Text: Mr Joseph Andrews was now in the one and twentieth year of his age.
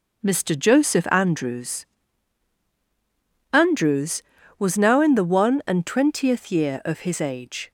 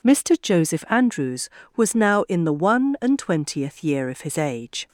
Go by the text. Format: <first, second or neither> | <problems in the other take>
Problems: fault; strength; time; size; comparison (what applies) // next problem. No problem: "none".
second | says "Andrews" twice; at 3.5 s